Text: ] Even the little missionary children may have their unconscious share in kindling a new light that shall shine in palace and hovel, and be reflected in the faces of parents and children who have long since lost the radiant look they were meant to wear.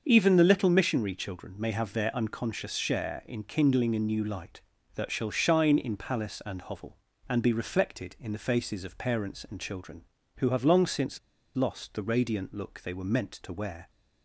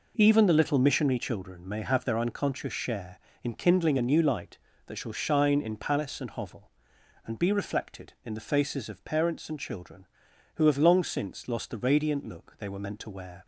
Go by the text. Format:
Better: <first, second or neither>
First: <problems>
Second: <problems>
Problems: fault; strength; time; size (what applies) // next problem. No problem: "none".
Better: second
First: starts louder than the rest; until 1.0 s; 6.5 dB // pauses between "since" and "lost"; at 11.1 s; 0.38 s long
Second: none